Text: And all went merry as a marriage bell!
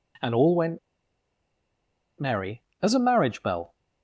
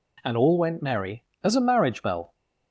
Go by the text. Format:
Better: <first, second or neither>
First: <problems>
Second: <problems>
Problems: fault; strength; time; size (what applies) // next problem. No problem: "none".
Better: second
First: pauses between "went" and "merry"; strong; at 0.7 s; 1.4 s long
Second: none